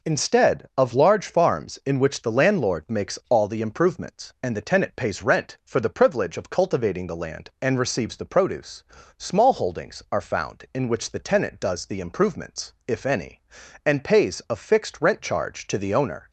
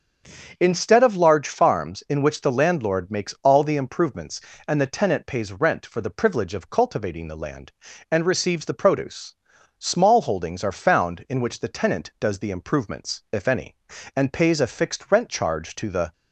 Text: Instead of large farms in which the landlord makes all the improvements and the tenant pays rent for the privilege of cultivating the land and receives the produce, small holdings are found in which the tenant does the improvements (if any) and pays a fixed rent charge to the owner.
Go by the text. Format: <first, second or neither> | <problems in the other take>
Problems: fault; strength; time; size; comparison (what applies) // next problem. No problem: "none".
first | starts louder than the rest; until 1.6 s; 7 dB // stops before "owner"; at 16.1 s